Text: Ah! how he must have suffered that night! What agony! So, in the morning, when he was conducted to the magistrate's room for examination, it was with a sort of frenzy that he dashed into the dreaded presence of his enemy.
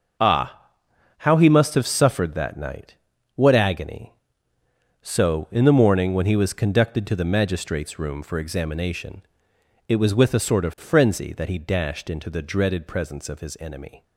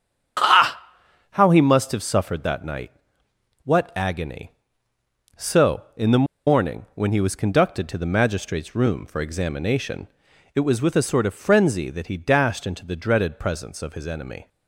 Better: first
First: starts louder than the rest; noticeable; until 1.6 s; 6 dB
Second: starts louder than the rest; strong; until 1.8 s; 8 dB // pauses between "the" and "morning"; slight; at 6.2 s; 0.22 s long

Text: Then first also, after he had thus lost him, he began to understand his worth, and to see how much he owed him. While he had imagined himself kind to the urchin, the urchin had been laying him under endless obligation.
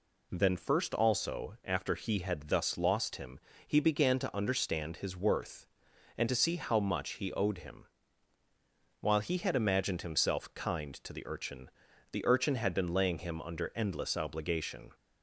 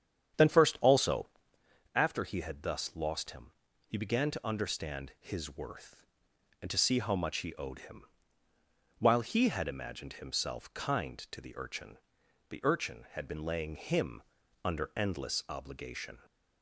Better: first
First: none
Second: starts louder than the rest; strong; until 1.8 s; 8.5 dB // pauses between "him" and "under"; at 14.2 s; 0.42 s long

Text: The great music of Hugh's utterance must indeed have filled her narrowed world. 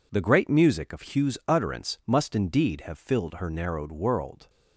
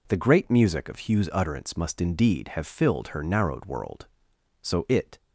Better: first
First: none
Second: goes on to say "So it"; from 4.6 s on; 0.56 s long

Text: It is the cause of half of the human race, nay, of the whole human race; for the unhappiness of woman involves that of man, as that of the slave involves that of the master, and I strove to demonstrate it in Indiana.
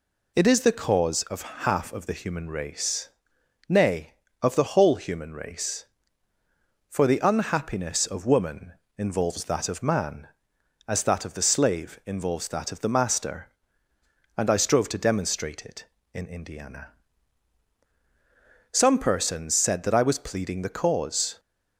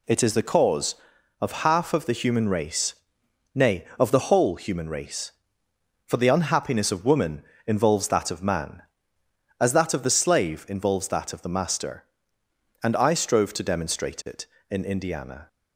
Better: second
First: pauses between "woman" and "involves"; slight; at 8.7 s; 0.24 s long // goes on to say "Some persons said that I was pleading the cause"; strong; from 18.7 s on; 2.6 s long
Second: pauses between "woman" and "involves"; slight; at 7.4 s; 0.24 s long

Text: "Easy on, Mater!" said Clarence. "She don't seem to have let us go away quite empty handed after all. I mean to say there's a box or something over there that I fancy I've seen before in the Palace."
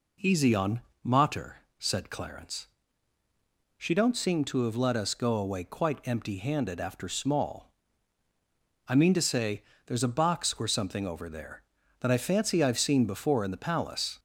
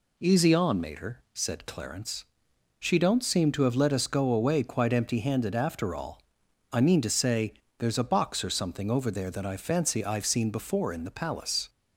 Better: second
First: says "small" for "all"; at 7.0 s // pauses between "say" and "there's"; slight; at 9.6 s; 0.22 s long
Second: pauses between "say" and "there's"; slight; at 7.5 s; 0.24 s long

